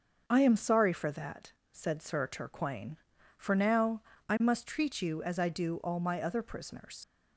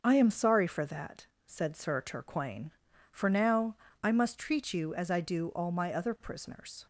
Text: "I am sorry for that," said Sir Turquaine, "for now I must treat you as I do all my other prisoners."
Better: second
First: starts louder than the rest; until 1.2 s; 6.5 dB // pauses between "now" and "I"; slight; at 4.0 s; 0.26 s long // leaves "prisoners" unfinished; at 7.0 s; 70 ms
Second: starts louder than the rest; until 1.0 s; 6.5 dB // pauses between "now" and "I"; slight; at 3.7 s; 0.26 s long

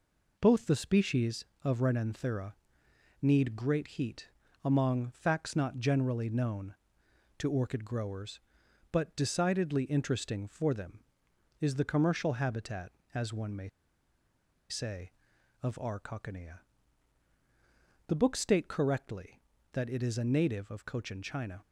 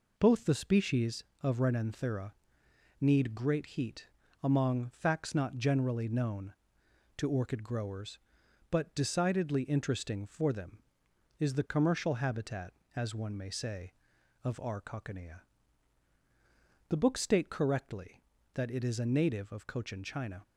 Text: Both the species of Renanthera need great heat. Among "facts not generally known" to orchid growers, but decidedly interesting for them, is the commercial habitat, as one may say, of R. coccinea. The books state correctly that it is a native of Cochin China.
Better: second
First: pauses between "Renanthera" and "need"; noticeable; at 2.5 s; 0.68 s long // pauses between "may" and "say"; at 13.6 s; 1.0 s long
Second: pauses between "Renanthera" and "need"; noticeable; at 2.3 s; 0.68 s long

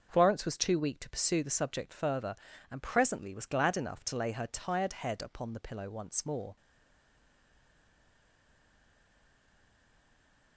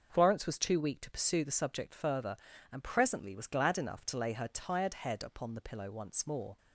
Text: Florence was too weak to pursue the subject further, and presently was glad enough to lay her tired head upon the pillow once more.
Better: second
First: starts louder than the rest; noticeable; until 1.1 s; 6 dB // stays silent after the last word; strong; from 6.5 s on; 4.0 s long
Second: starts louder than the rest; noticeable; until 1.1 s; 6 dB

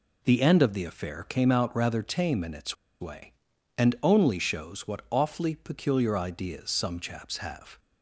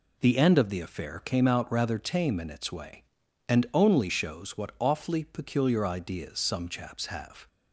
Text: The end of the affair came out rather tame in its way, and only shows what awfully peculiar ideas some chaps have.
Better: second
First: pauses between "its" and "way"; slight; at 2.7 s; 0.25 s long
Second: none

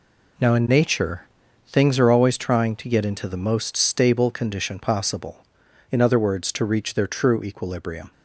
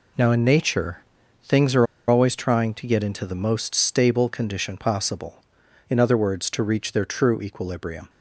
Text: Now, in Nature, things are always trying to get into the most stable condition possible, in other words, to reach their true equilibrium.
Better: first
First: none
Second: pauses between "are" and "always"; slight; at 1.8 s; 0.23 s long

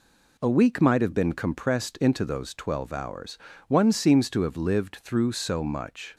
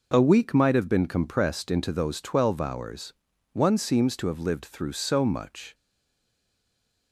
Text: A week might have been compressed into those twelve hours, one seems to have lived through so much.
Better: first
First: none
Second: stays silent after the last word; noticeable; from 5.7 s on; 1.4 s long

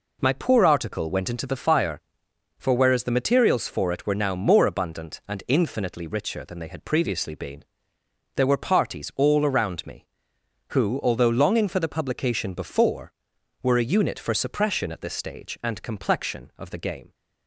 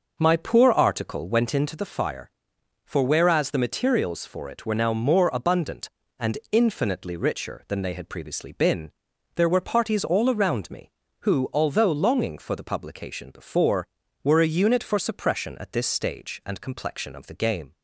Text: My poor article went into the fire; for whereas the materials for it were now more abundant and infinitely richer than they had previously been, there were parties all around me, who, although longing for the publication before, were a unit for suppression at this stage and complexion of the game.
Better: first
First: none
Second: starts louder than the rest; noticeable; until 1.5 s; 6 dB

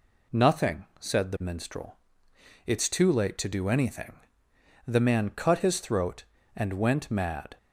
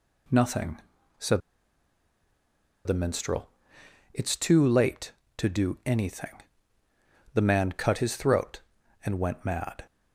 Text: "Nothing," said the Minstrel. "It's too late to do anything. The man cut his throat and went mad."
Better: first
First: none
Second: pauses between "said" and "the"; strong; at 1.4 s; 1.4 s long

